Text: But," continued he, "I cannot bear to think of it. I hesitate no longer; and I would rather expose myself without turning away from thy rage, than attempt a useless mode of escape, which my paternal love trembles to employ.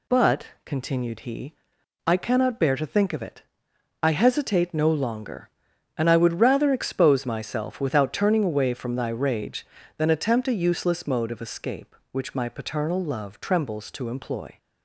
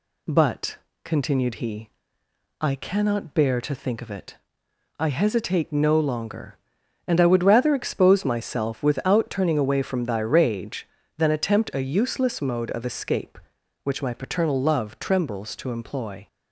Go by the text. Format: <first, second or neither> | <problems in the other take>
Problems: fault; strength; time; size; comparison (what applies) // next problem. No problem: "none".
neither | none